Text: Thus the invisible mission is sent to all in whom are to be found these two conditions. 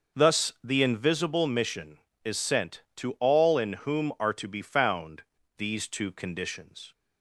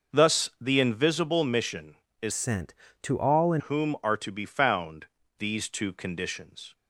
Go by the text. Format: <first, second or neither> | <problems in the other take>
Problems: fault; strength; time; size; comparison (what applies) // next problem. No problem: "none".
first | starts louder than the rest; noticeable; until 1.2 s; 6 dB; also in the first // changes voice from "sent" to "in"; from 2.3 to 3.6 s; 1.3 s long // pauses between "found" and "these"; slight; at 5.0 s; 0.34 s long; also in the first